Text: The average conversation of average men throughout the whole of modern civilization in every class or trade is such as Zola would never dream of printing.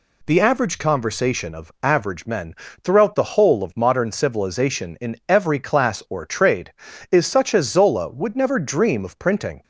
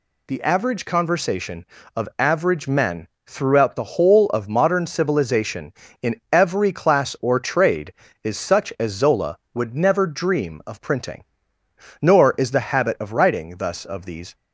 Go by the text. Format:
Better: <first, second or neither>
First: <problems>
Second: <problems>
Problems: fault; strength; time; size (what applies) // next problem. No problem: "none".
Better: first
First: pauses between "men" and "throughout"; slight; at 2.5 s; 0.30 s long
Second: pauses between "men" and "throughout"; slight; at 3.0 s; 0.22 s long // goes on to say "Nor is the habit of writing thus of these"; strong; from 12.0 s on; 2.3 s long